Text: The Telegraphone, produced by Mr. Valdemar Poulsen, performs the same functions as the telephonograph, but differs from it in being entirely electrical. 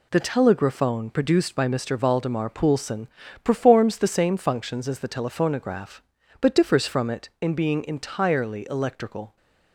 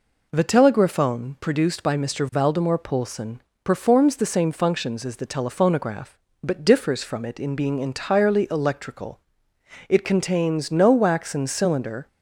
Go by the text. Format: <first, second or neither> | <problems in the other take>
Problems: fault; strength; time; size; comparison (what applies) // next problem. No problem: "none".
first | goes on to say "It contains no waxen cylinder"; strong; from 9.8 s on; 2.1 s long